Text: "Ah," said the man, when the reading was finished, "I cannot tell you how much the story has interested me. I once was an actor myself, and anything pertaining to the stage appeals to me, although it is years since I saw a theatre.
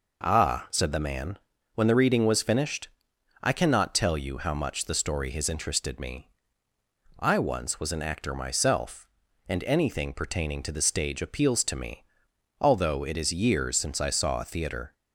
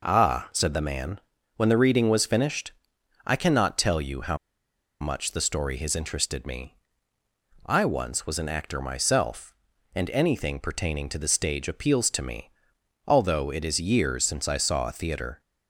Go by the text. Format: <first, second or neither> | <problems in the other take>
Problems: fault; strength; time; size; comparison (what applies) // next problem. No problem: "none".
first | pauses between "how" and "much"; noticeable; at 4.3 s; 0.65 s long